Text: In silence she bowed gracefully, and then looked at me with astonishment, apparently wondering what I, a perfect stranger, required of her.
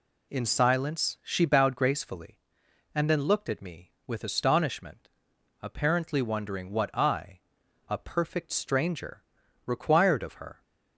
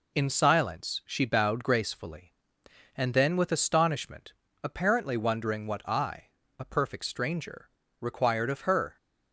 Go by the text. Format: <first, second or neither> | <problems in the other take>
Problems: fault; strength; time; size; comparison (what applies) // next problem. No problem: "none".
first | skips "looked at me"; at 3.3 s